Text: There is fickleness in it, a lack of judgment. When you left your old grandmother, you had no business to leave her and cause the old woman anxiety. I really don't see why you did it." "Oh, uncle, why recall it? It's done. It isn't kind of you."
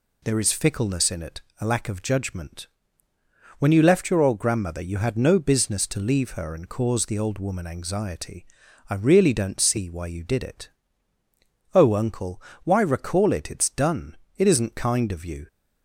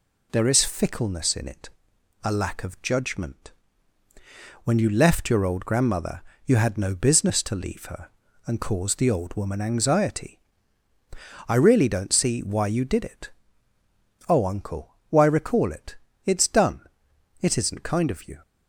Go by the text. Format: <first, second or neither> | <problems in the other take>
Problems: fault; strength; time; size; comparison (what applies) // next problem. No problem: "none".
neither | none